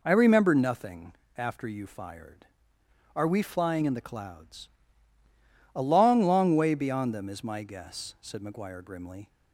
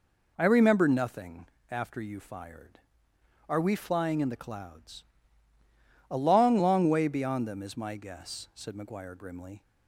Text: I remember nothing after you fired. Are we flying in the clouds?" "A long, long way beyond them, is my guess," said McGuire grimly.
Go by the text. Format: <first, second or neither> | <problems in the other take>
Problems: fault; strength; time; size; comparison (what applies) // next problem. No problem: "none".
neither | pauses between "nothing" and "after"; slight; the same in both